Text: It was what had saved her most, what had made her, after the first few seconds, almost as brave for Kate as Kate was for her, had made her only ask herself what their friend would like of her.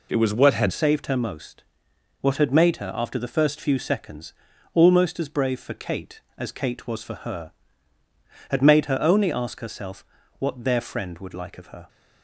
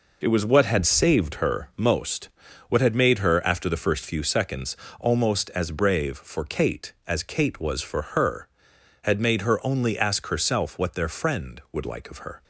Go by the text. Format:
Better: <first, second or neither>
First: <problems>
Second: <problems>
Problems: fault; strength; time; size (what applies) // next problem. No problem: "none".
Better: second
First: changes voice at "saved"; from 0.6 s on; 11.2 s long // pauses between "herself" and "what"; slight; at 10.0 s; 0.34 s long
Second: none